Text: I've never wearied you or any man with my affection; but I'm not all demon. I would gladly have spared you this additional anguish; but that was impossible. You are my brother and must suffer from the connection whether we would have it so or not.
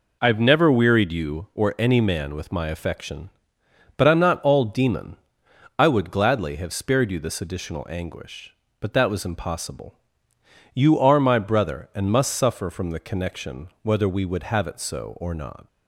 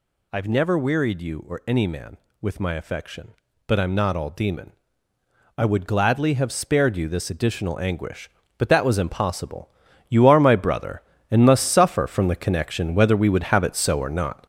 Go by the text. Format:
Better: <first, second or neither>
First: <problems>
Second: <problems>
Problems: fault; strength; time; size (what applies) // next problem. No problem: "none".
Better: first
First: none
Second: gets louder; throughout; 6.5 dB